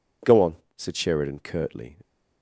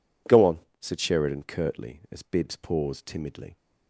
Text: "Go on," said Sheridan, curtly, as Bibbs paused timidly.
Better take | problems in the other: second | stops before "as Bibbs paused timidly"; at 2.0 s

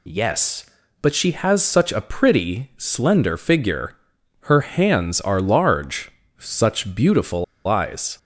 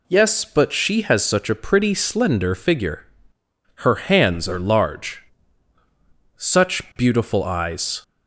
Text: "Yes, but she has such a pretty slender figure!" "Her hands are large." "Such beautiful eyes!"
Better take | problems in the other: second | pauses between "beautiful" and "eyes"; slight; at 7.4 s; 0.21 s long

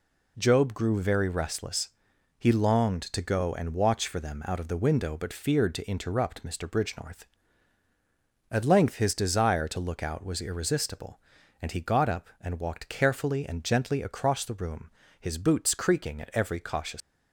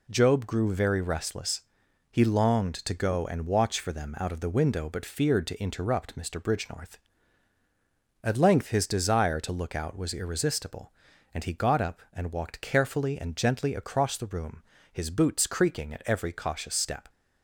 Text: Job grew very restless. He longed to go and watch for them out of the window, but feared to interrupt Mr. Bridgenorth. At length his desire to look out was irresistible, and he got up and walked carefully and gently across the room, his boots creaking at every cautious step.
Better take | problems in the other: second | stops before "step"; at 17.0 s

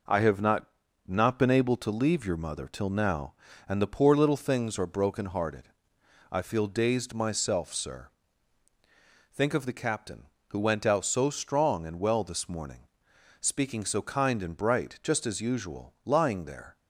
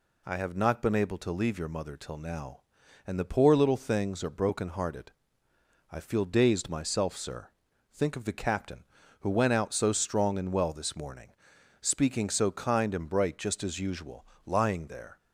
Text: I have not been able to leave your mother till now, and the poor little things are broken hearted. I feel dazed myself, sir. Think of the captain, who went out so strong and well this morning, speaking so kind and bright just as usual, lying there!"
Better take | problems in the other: second | says "not" twice; at 1.0 s

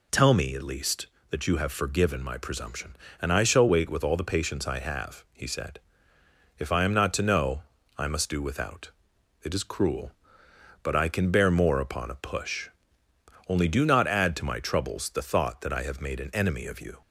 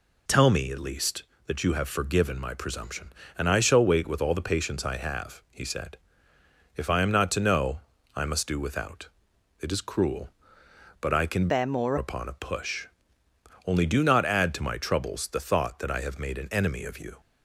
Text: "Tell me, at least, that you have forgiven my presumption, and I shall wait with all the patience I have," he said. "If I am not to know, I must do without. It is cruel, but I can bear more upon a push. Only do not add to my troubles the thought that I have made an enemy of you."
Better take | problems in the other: first | changes voice from "bear" to "more"; from 11.4 to 11.9 s; 0.5 s long

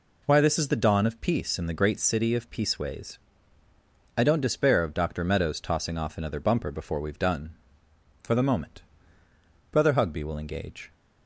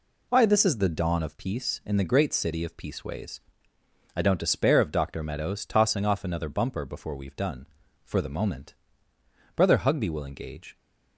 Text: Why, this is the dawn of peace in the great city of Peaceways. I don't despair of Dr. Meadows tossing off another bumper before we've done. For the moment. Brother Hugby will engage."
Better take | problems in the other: neither | none

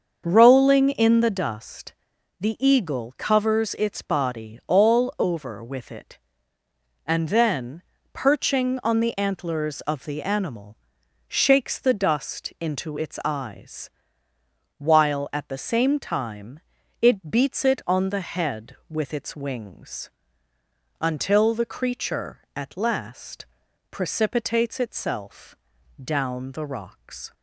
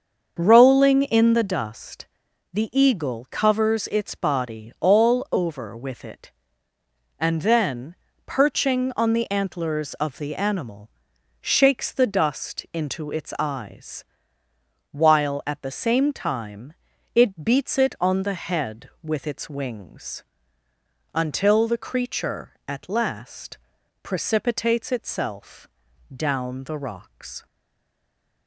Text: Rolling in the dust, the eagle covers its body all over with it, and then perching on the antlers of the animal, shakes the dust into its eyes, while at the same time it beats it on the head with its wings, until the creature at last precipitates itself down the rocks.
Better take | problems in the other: first | starts louder than the rest; until 1.4 s; 6.5 dB; also in the first // pauses between "then" and "perching"; slight; at 7.9 s; 0.32 s long; slight in the first // pauses between "time" and "it"; at 16.7 s; 0.40 s long; also in the first // pauses between "last" and "precipitates"; noticeable; at 23.5 s; 0.46 s long; noticeable in the first // pauses between "itself" and "down"; at 25.6 s; 0.44 s long; also in the first // stays silent after the last word; from 27.4 s on; 1.0 s long

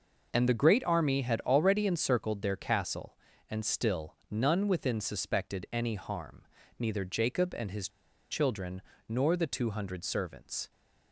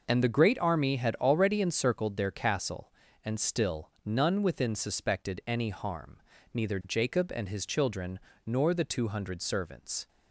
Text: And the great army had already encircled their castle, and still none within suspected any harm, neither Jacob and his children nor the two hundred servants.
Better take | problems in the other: second | pauses between "his" and "children"; at 7.8 s; 0.42 s long // pauses between "children" and "nor"; slight; at 8.8 s; 0.28 s long; slight in the second

